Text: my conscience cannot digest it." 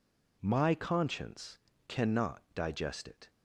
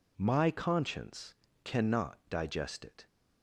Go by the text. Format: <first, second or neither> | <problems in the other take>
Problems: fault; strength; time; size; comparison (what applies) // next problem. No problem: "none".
neither | pauses between "conscience" and "cannot"; slight; the same in both